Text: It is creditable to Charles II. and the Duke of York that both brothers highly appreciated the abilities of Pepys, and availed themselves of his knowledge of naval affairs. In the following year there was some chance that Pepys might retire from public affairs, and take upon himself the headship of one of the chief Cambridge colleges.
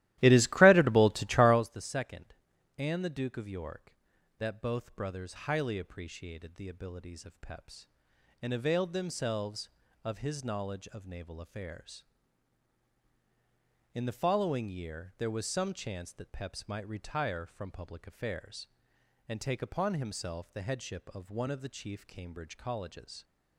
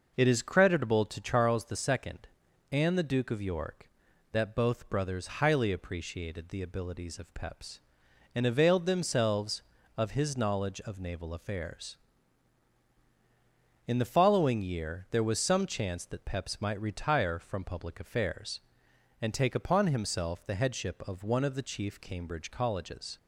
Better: second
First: starts louder than the rest; strong; until 1.6 s; 15.5 dB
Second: none

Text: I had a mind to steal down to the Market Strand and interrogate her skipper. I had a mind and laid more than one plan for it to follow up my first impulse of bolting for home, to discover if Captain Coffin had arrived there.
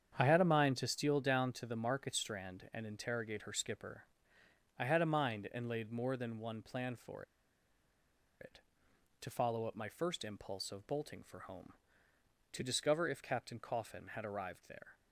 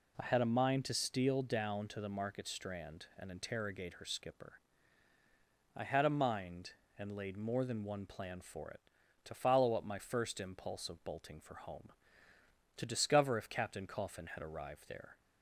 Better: second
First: starts louder than the rest; strong; until 1.1 s; 8 dB // pauses between "for" and "it"; at 7.2 s; 1.1 s long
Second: none

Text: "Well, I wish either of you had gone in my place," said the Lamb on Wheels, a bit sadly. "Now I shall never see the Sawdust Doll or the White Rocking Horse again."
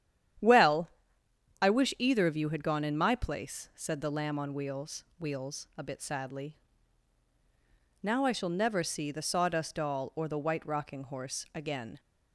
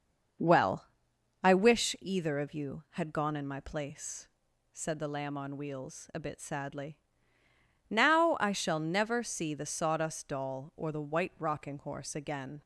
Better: second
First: starts louder than the rest; strong; until 2.1 s; 10 dB // says "Wheels" twice; at 5.1 s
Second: starts louder than the rest; noticeable; until 1.9 s; 6 dB

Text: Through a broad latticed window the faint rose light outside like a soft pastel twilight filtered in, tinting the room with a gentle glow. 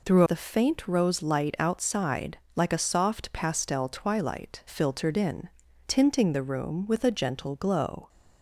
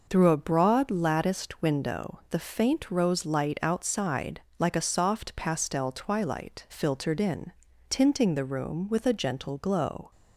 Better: second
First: skips "a broad latticed window"; at 0.2 s // pauses between "outside" and "like"; slight; at 2.3 s; 0.18 s long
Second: pauses between "outside" and "like"; slight; at 4.3 s; 0.18 s long

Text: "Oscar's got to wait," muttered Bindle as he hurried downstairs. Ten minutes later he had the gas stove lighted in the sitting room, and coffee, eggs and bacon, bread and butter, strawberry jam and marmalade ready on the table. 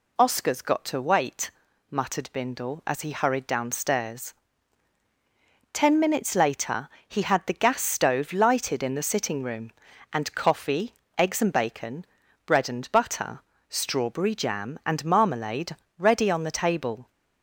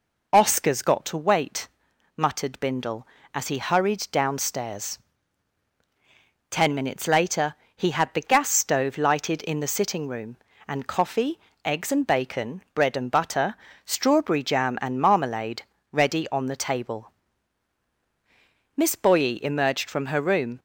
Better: first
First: pauses between "later" and "he"; slight; at 6.8 s; 0.18 s long // pauses between "marmalade" and "ready"; slight; at 15.7 s; 0.22 s long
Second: pauses between "later" and "he"; slight; at 7.5 s; 0.22 s long // pauses between "marmalade" and "ready"; slight; at 15.6 s; 0.30 s long // goes on to say "Miss Boye emerged from her room"; strong; from 18.7 s on; 1.8 s long

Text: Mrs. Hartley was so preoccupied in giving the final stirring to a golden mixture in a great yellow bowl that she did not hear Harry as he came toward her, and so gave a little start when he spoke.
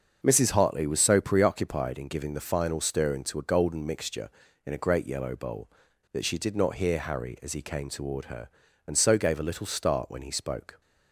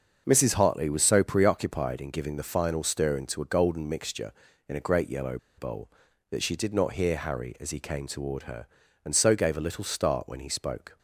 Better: first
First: starts louder than the rest; until 1.2 s; 6 dB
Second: starts louder than the rest; until 1.2 s; 6 dB // pauses between "yellow" and "bowl"; slight; at 5.3 s; 0.19 s long

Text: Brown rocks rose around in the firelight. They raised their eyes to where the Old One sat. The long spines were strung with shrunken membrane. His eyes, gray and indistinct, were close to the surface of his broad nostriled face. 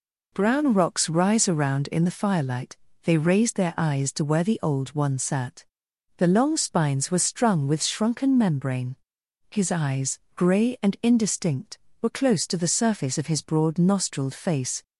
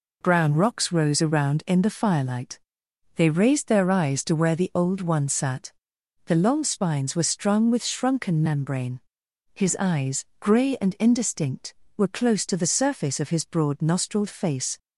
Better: second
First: says "rise" for "rose"; at 1.1 s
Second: none

